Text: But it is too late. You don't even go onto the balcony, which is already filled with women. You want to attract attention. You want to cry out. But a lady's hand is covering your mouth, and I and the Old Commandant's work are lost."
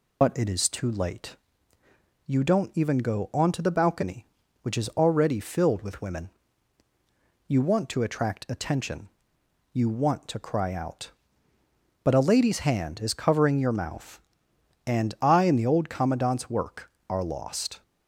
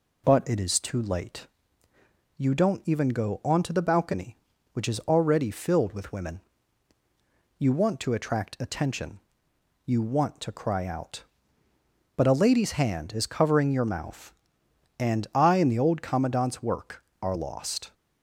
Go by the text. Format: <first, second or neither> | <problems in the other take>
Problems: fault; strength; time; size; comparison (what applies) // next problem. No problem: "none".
second | loses the start of "But"; at 0.2 s; 70 ms